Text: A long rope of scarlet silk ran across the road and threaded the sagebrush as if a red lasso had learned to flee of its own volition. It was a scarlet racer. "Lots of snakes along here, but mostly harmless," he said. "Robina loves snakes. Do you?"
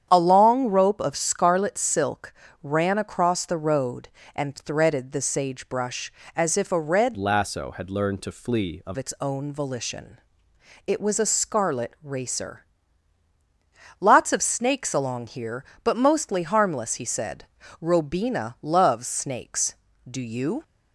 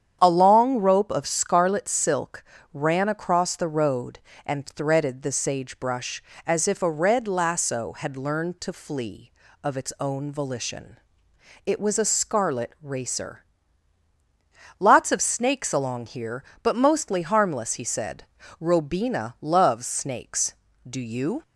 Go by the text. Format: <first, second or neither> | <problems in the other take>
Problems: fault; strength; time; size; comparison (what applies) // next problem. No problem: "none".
second | starts louder than the rest; strong; until 1.1 s; 9 dB; strong in the second // pauses between "silk" and "ran"; slight; at 2.3 s; 0.30 s long; slight in the second // changes voice from "lasso" to "of"; from 7.1 to 8.9 s; 1.8 s long